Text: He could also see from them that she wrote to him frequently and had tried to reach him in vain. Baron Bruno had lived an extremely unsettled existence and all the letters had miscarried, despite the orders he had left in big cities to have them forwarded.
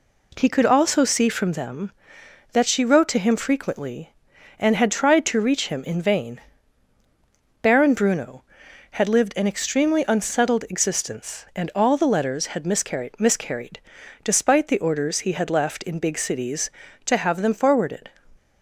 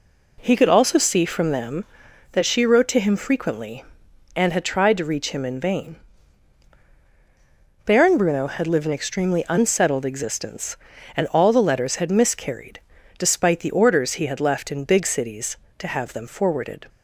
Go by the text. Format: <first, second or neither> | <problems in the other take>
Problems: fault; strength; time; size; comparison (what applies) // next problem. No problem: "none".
second | says "miscarried" twice; at 13.1 s